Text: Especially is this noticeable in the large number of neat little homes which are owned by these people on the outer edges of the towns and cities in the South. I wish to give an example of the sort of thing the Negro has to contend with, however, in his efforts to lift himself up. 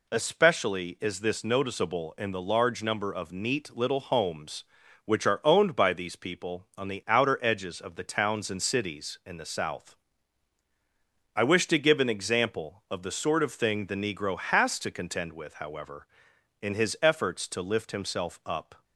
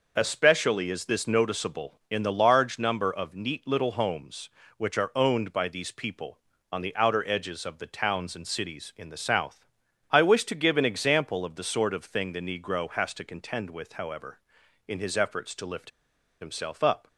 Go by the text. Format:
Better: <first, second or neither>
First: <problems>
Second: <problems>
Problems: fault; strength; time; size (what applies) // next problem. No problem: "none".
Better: first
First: none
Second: pauses between "lift" and "himself"; noticeable; at 15.9 s; 0.50 s long